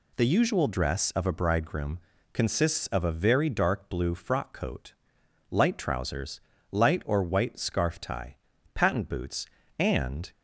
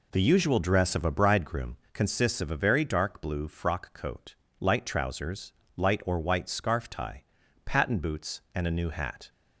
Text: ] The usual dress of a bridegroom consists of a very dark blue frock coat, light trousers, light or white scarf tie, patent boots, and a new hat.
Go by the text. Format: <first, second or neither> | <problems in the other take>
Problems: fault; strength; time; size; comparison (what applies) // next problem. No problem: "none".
second | pauses between "bridegroom" and "consists"; slight; at 1.9 s; 0.34 s long; slight in the second // stops before "a new hat"; at 10.3 s